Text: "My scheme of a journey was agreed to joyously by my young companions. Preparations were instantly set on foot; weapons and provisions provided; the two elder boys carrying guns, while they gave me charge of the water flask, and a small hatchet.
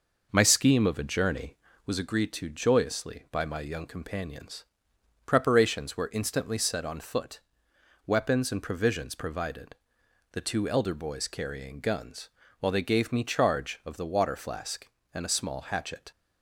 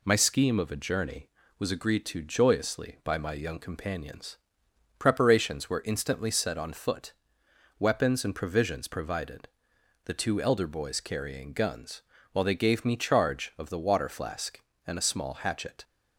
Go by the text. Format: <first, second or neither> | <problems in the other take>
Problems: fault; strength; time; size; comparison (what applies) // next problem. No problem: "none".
second | starts louder than the rest; noticeable; until 1.9 s; 5.5 dB